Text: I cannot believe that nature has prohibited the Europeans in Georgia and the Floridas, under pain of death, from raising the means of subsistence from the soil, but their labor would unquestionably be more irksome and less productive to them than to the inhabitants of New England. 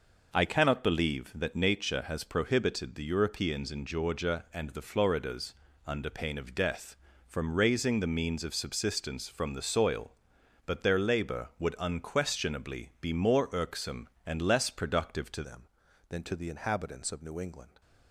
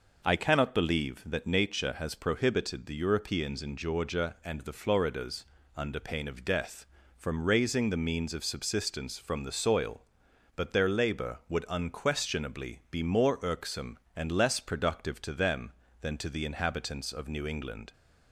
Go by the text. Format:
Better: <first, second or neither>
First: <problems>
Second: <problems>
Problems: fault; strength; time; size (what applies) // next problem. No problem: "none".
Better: second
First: changes voice at "them"; from 15.4 s on; 2.4 s long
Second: none